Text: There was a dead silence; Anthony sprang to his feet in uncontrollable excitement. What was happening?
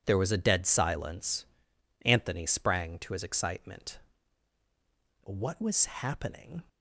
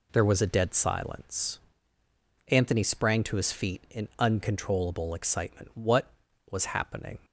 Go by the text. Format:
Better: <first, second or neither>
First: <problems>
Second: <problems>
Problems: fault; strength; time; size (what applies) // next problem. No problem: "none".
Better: second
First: skips "feet in uncontrollable"; at 3.2 s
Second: none